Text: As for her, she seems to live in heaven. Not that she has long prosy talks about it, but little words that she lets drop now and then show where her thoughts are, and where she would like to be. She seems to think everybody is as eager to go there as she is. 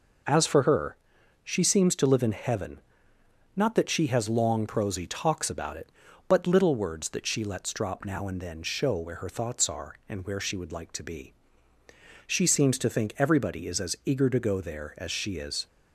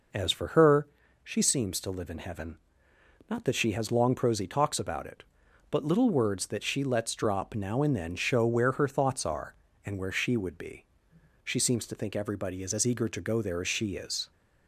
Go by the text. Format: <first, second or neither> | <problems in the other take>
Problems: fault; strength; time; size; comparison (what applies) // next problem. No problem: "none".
first | skips "like to"; at 10.5 s